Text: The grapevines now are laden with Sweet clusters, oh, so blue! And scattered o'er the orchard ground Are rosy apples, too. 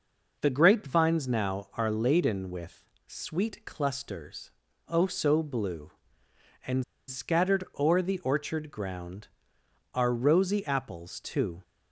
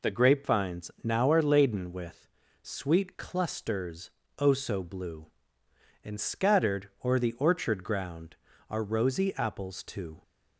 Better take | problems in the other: second | pauses between "with" and "Sweet"; slight; at 2.8 s; 0.24 s long; slight in the second // pauses between "And" and "scattered"; slight; at 6.8 s; 0.26 s long // pauses between "scattered" and "o'er"; slight; at 7.6 s; 0.16 s long; slight in the second

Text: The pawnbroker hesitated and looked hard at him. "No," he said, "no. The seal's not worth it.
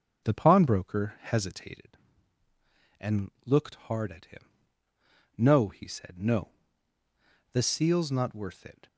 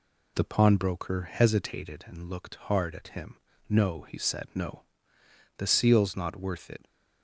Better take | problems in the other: second | starts louder than the rest; noticeable; until 1.9 s; 5.5 dB

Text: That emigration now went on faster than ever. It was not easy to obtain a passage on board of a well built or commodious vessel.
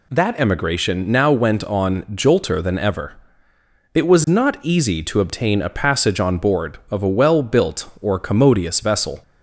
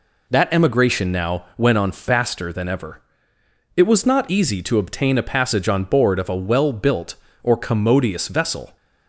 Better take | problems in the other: second | says "jolter" for "faster"; at 2.0 s

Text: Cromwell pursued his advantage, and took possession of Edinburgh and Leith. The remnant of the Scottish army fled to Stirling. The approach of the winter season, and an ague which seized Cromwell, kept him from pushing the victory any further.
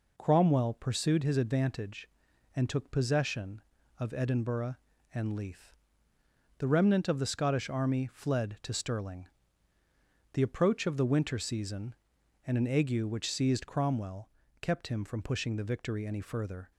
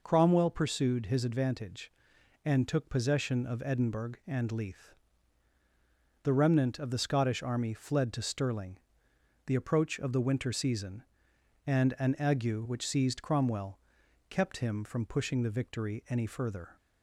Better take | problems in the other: neither | none

